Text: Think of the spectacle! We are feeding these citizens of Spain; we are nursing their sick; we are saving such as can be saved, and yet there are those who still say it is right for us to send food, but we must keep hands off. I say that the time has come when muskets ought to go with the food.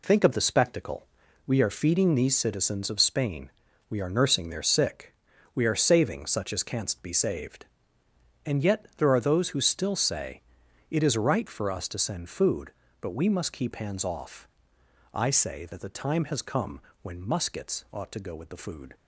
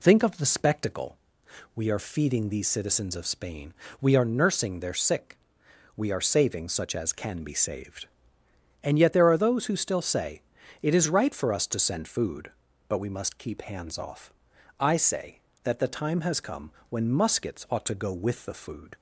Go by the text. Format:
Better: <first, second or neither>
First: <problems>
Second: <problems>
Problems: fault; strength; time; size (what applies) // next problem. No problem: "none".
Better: second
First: says "canst" for "can"; at 6.6 s // pauses between "say" and "it"; noticeable; at 10.4 s; 0.48 s long // pauses between "come" and "when"; slight; at 16.7 s; 0.22 s long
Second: pauses between "say" and "it"; at 10.3 s; 0.42 s long // pauses between "come" and "when"; slight; at 16.7 s; 0.16 s long